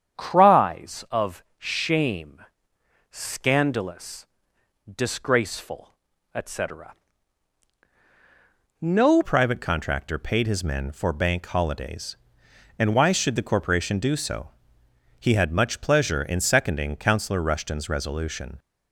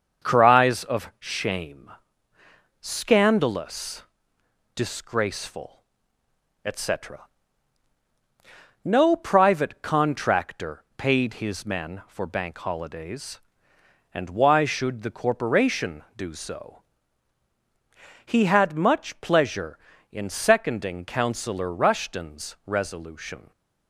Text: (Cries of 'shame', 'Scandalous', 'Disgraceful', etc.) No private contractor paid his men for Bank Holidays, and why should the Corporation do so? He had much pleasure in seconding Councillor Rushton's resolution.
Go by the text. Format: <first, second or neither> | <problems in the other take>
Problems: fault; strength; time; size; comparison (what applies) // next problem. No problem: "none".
second | starts louder than the rest; strong; until 1.2 s; 8 dB; also in the second // changes voice at "private"; from 9.2 s on; 9.3 s long